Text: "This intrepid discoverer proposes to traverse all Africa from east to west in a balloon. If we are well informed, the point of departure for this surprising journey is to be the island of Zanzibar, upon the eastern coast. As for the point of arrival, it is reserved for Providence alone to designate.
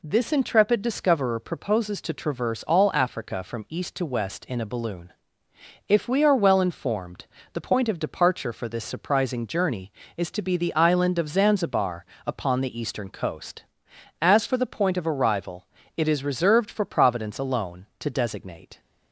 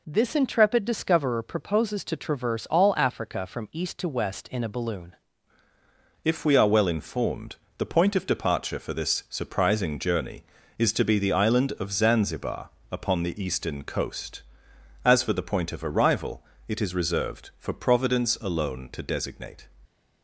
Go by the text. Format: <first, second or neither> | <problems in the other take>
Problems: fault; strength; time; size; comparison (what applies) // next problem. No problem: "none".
first | changes voice at "If"; from 6.2 s on; 13.4 s long